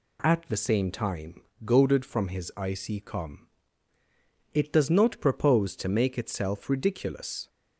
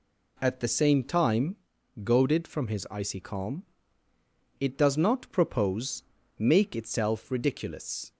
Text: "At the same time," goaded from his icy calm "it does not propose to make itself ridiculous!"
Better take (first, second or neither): first